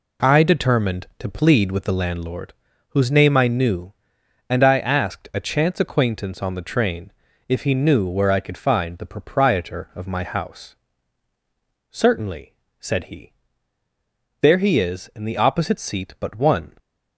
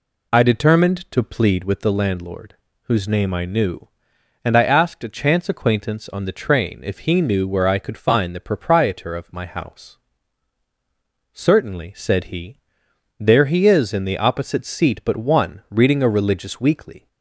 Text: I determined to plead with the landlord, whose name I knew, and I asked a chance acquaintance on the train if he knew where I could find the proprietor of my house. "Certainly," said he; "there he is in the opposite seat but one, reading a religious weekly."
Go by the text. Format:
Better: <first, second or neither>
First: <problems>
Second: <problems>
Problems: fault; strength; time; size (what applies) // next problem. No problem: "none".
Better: second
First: pauses between "train" and "if"; at 7.1 s; 0.38 s long // stops before "reading a religious weekly"; at 16.7 s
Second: none